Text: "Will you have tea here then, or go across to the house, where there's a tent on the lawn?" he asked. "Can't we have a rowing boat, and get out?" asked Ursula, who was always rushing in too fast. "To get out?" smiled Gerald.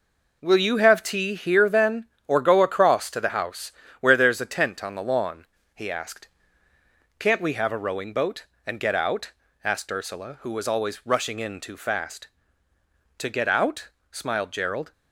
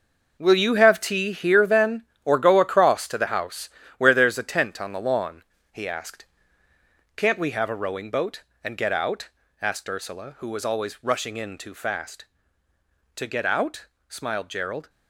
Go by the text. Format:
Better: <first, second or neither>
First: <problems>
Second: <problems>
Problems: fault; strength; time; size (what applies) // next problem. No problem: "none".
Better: first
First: none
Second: gets quieter; strong; throughout; 11 dB